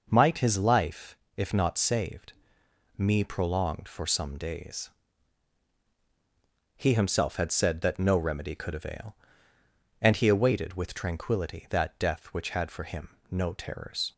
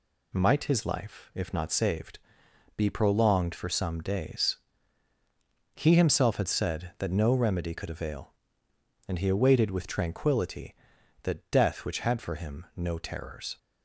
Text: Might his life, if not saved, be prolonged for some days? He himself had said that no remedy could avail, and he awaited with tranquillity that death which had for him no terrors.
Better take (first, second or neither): second